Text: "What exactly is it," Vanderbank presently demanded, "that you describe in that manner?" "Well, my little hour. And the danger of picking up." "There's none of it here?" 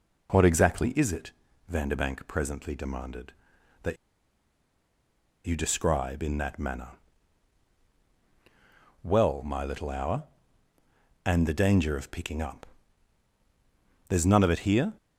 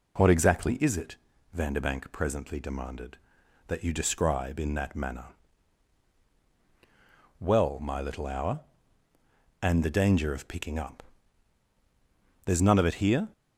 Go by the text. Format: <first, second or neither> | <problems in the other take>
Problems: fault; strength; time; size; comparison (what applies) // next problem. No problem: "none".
second | pauses between "that" and "you"; strong; at 3.9 s; 1.5 s long